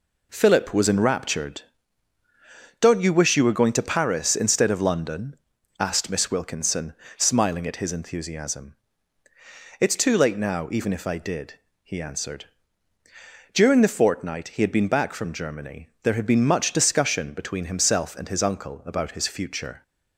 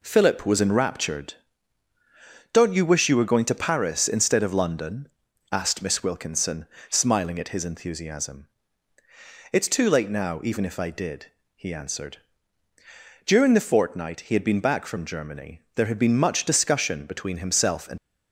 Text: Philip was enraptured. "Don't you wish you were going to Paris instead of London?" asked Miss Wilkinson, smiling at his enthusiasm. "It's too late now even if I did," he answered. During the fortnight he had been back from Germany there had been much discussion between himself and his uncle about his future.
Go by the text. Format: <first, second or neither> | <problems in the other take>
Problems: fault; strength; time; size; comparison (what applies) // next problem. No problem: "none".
first | pauses between "Germany" and "there"; slight; at 15.6 s; 0.16 s long; slight in the first // stops before "his uncle about his future"; at 17.9 s